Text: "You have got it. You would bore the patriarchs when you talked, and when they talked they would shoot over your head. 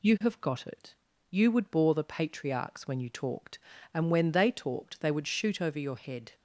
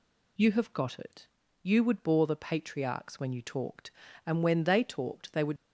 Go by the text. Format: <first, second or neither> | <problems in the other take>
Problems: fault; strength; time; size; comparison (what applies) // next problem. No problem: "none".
first | stops before "shoot over your head"; at 5.5 s